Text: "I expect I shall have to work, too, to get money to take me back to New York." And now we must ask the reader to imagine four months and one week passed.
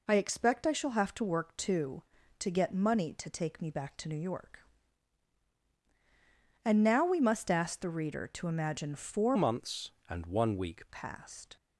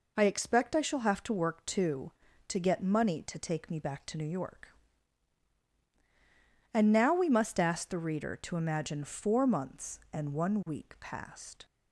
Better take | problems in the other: second | changes voice from "months" to "week"; from 9.3 to 10.8 s; 1.5 s long

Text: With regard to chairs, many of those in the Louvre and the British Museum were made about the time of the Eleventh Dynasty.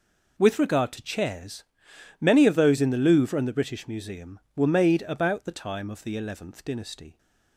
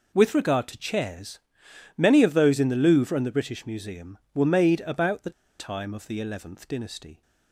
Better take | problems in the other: first | pauses between "the" and "time"; slight; at 5.3 s; 0.28 s long

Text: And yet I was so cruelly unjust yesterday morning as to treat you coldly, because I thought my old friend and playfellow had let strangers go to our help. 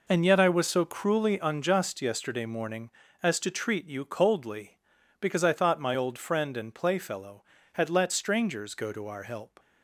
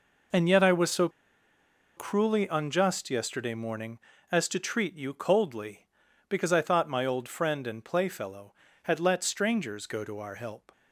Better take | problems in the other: first | pauses between "so" and "cruelly"; noticeable; at 1.0 s; 0.88 s long

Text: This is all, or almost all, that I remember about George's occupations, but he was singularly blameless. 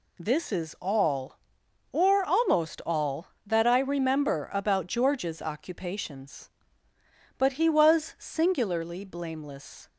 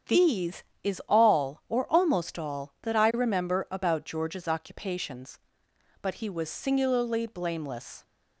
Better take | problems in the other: first | starts louder than the rest; strong; until 1.3 s; 8 dB // says "These" for "This"; at 0.0 s

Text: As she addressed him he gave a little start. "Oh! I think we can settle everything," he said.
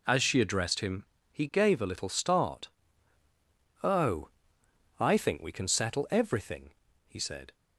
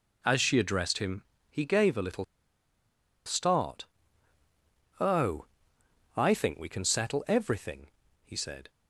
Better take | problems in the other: first | pauses between "him" and "he"; slight; at 1.2 s; 0.26 s long; slight in the first // pauses between "little" and "start"; at 2.2 s; 1.0 s long

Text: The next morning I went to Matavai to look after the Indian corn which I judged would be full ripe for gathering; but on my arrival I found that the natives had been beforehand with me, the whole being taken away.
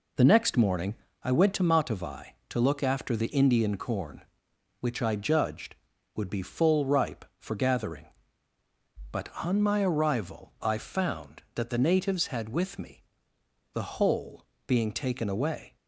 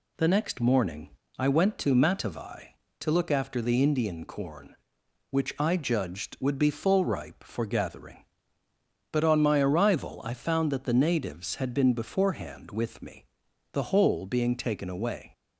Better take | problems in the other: second | pauses between "morning" and "I"; slight; at 0.9 s; 0.28 s long; slight in the second // skips "been beforehand"; at 12.4 s // pauses between "whole" and "being"; slight; at 14.4 s; 0.24 s long

